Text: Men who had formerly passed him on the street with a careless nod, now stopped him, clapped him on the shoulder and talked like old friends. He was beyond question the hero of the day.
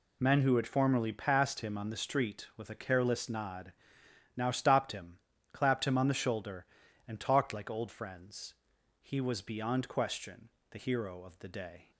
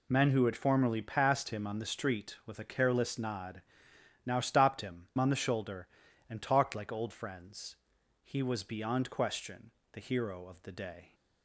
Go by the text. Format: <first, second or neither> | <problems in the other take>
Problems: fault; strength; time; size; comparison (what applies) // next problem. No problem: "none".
first | skips "clapped him"; at 5.1 s // pauses between "question" and "the"; slight; at 9.7 s; 0.22 s long; slight in the first